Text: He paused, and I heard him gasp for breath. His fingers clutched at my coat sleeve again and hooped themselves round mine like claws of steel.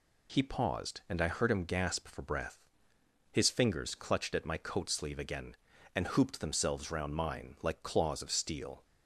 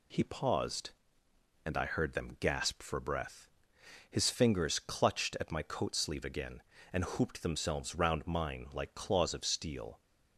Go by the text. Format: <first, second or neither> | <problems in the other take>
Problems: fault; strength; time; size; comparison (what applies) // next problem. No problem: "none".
first | says "them" for "him"; at 2.1 s